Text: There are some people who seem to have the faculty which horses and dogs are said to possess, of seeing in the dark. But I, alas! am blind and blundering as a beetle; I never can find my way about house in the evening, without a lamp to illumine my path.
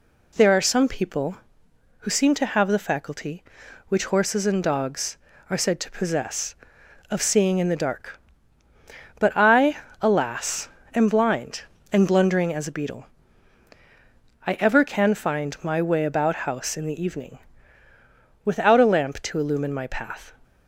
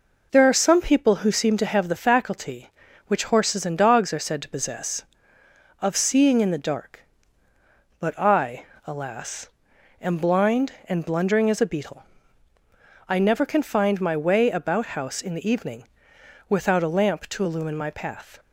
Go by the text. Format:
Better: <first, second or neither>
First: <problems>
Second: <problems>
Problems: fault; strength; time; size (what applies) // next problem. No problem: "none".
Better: second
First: says "ever" for "never"; at 14.6 s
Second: none